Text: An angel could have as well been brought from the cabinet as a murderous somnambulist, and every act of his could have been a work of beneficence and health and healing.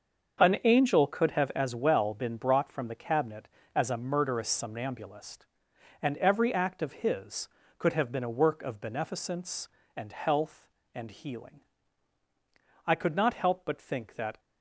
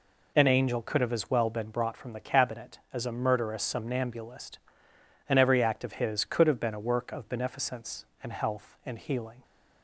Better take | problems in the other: second | starts louder than the rest; until 1.4 s; 6.5 dB // goes on to say "I could not help but think that"; from 12.8 s on; 1.5 s long

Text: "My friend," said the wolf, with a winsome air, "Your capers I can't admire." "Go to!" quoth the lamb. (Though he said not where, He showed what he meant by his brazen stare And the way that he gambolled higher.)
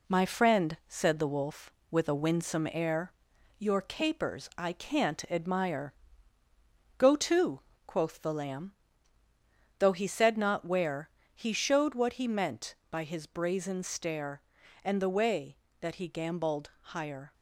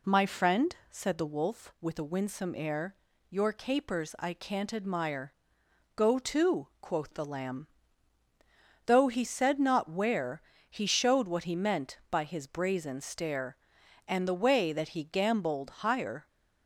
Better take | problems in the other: second | gets quieter; throughout; 4 dB

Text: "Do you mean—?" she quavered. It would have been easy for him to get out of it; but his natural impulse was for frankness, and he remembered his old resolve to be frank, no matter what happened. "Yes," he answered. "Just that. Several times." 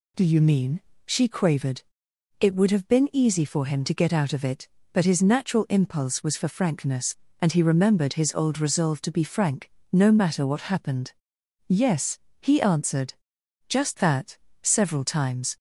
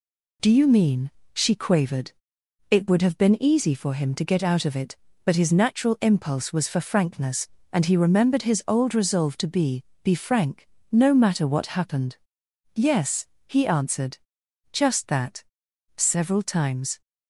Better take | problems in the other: first | says "be" twice; at 10.0 s

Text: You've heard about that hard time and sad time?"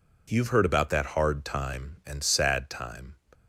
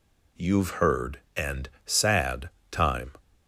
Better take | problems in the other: first | skips "about that hard time"; at 1.2 s // pauses between "and" and "sad"; slight; at 1.6 s; 0.16 s long // pauses between "sad" and "time"; slight; at 2.4 s; 0.22 s long

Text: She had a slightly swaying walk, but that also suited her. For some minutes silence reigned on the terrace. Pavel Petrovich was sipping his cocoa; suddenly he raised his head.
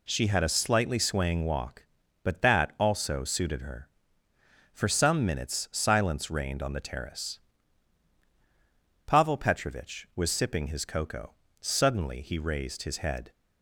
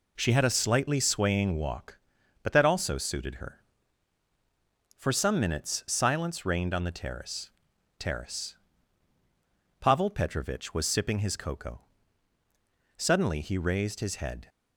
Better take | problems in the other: first | says "terrace" twice; at 7.9 s

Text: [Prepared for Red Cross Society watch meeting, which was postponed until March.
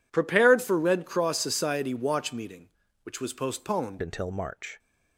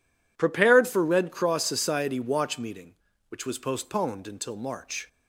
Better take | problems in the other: second | changes voice at "until"; from 4.0 s on; 0.7 s long

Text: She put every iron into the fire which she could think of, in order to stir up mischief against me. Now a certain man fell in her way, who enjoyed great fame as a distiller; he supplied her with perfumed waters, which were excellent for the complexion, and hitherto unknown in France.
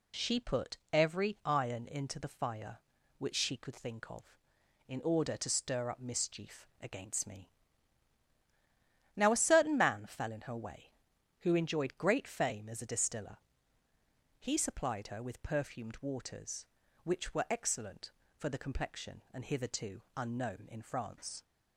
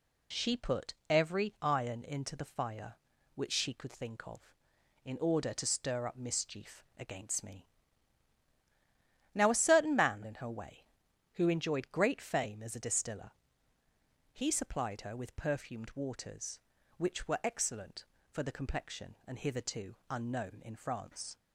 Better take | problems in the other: first | pauses between "put" and "every"; slight; at 0.9 s; 0.16 s long; slight in the first // skips "fell"; at 10.2 s

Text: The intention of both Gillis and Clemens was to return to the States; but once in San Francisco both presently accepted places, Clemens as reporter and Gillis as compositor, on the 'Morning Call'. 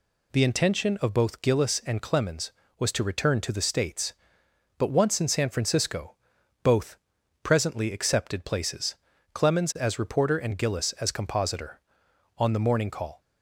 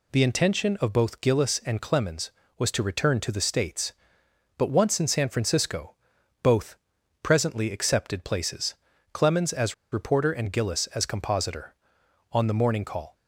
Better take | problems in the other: first | pauses between "Francisco" and "both"; noticeable; at 5.9 s; 0.48 s long; noticeable in the first // pauses between "both" and "presently"; at 6.7 s; 0.44 s long; also in the first // pauses between "as" and "reporter"; slight; at 9.7 s; 0.18 s long

